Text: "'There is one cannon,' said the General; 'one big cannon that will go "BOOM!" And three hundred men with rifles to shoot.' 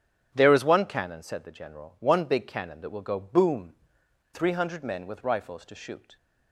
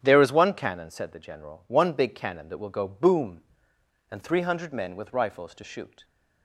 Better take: second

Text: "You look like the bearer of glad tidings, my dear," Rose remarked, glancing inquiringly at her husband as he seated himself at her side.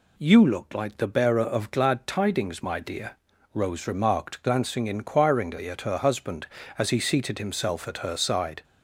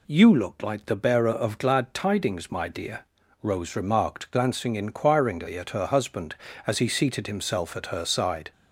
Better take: neither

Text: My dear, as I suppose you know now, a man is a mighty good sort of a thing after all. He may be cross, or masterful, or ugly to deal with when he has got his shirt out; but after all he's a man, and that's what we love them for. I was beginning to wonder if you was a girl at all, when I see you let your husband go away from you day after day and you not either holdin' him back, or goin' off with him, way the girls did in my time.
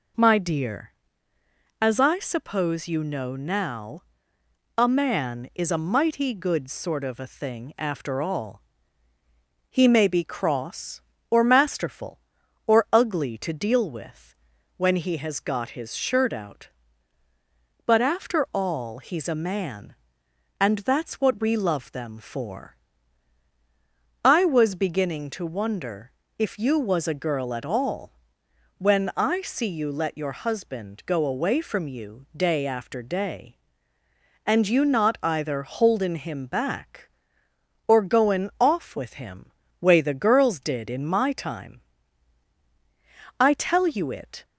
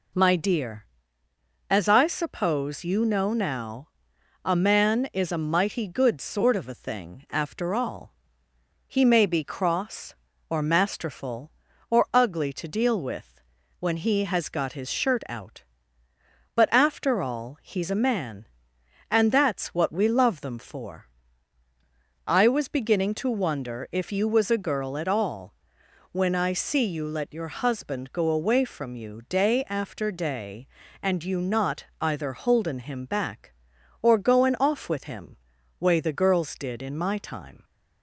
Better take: second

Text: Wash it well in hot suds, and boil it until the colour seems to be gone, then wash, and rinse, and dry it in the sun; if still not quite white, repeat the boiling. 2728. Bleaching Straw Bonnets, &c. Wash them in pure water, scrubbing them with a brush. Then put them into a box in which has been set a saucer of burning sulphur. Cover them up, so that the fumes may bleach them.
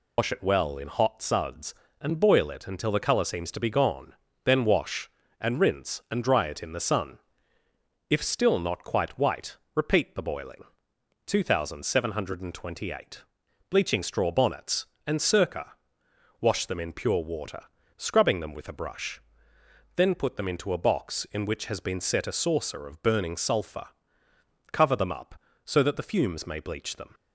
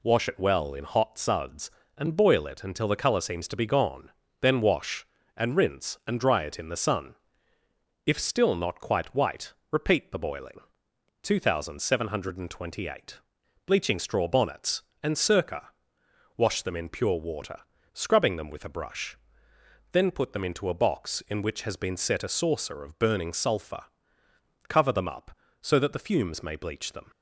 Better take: second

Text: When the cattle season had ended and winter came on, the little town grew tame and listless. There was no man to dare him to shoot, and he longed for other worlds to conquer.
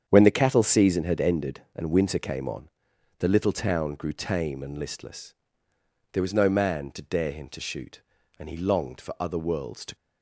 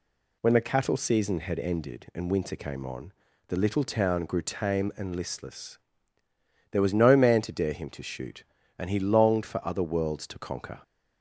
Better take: second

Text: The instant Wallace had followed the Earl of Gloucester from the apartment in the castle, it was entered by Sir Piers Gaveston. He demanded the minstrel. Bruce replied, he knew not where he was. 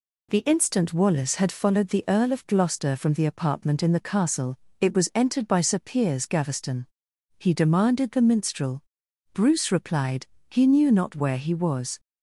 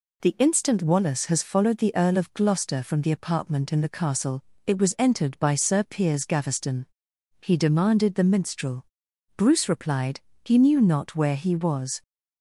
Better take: first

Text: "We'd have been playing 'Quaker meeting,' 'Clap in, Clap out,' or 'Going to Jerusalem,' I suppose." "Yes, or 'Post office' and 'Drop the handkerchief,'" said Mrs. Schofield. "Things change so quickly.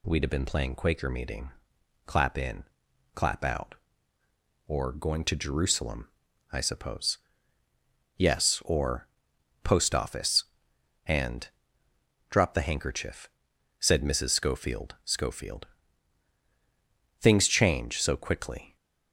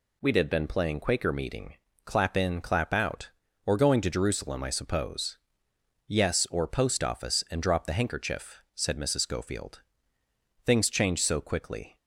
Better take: second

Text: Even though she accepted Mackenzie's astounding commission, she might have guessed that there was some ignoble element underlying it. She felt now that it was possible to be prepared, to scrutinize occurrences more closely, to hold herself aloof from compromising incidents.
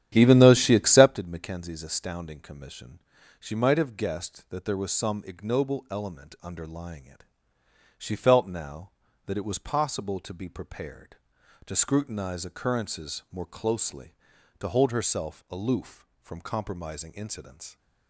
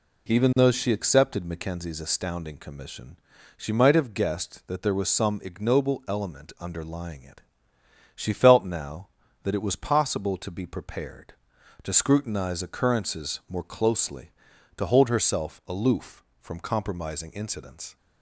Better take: second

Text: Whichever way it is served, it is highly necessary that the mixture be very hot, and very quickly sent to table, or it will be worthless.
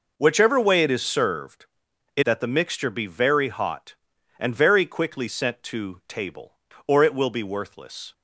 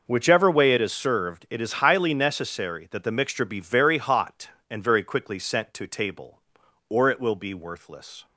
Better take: second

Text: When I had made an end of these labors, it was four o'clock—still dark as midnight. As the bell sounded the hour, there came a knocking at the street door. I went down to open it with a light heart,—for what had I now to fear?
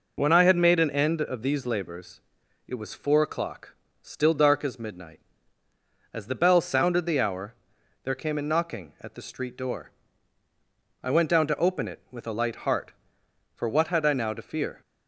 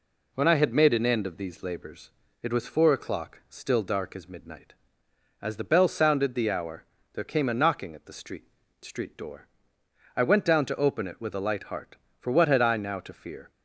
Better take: first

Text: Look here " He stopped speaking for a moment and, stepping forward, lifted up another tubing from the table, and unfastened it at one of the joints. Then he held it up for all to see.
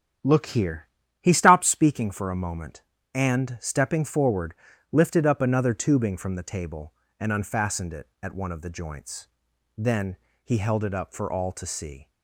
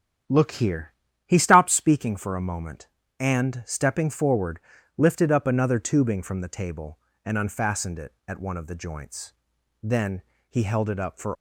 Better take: first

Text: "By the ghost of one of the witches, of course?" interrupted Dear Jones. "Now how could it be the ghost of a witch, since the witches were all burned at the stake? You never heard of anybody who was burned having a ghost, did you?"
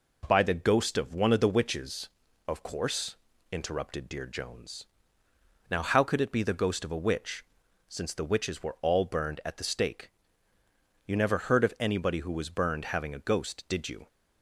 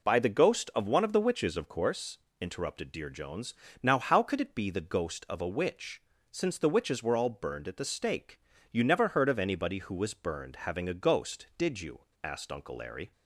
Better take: first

